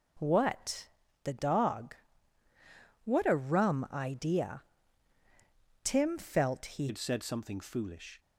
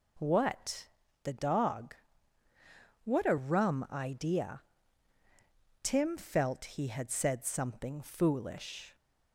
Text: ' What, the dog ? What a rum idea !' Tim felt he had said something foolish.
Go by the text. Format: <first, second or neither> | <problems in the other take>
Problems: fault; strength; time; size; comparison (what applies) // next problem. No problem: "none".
second | changes voice at "had"; from 6.8 s on; 1.3 s long